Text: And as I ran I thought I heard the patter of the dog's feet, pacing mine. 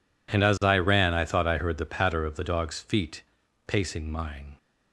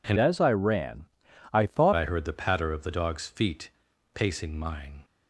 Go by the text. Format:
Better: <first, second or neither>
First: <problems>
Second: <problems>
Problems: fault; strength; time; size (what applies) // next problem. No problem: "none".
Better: first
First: none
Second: changes voice from "as" to "thought"; from 0.1 to 1.9 s; 1.8 s long // pauses between "ran" and "I"; at 1.0 s; 0.44 s long